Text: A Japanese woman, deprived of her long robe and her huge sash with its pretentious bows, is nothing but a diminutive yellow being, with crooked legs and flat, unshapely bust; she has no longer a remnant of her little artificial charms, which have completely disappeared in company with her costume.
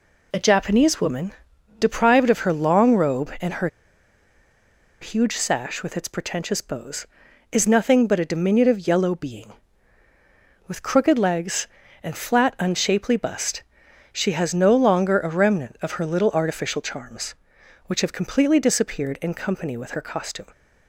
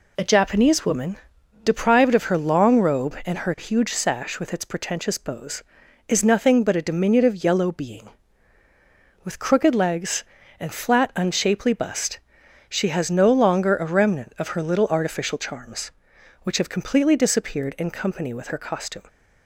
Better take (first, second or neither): second